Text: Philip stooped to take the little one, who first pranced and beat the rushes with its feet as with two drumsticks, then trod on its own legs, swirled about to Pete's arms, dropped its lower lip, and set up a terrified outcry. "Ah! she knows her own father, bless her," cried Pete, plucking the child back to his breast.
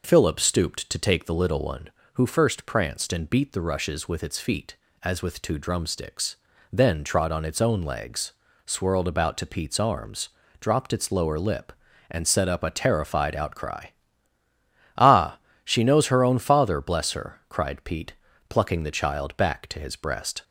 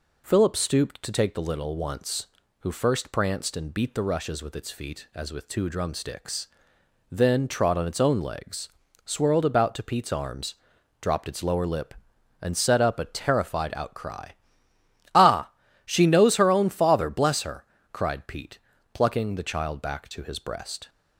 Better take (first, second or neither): first